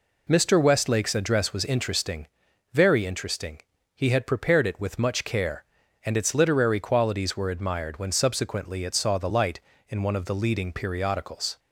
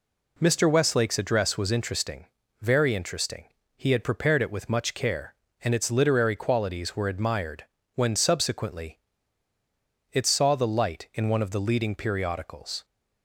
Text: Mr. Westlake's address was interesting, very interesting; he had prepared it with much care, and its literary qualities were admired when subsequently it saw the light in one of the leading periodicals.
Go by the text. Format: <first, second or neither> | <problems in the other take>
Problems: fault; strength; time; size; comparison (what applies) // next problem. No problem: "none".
first | pauses between "admired" and "when"; slight; at 7.6 s; 0.32 s long // pauses between "subsequently" and "it"; at 8.9 s; 1.1 s long